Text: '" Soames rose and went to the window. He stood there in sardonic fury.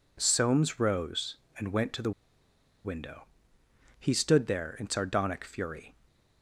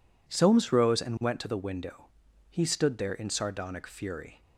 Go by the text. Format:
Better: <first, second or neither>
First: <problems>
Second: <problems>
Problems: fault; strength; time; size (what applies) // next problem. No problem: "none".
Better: second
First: pauses between "the" and "window"; noticeable; at 2.1 s; 0.74 s long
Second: none